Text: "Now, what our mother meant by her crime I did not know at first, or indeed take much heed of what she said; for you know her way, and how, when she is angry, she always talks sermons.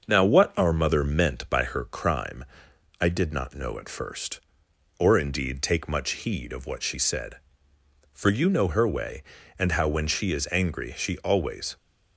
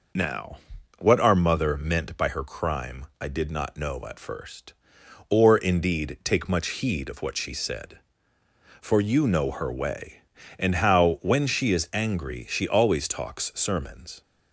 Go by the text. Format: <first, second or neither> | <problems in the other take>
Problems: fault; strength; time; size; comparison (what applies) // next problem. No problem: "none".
second | starts louder than the rest; until 1.0 s; 6.5 dB // pauses between "crime" and "I"; noticeable; at 2.4 s; 0.58 s long; slight in the second // stops before "talks sermons"; at 11.7 s